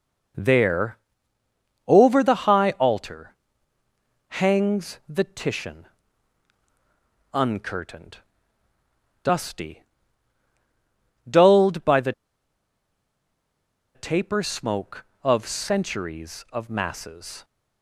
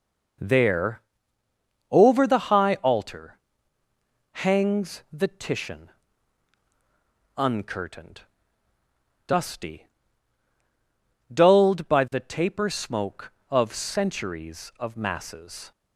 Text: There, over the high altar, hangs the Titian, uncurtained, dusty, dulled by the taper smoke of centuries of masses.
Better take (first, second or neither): second